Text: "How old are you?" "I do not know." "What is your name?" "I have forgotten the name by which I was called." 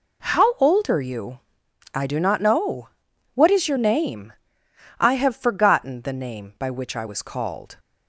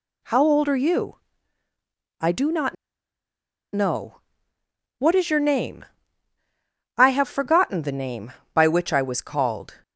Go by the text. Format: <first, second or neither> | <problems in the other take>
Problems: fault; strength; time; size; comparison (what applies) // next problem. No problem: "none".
first | pauses between "not" and "know"; at 2.7 s; 0.98 s long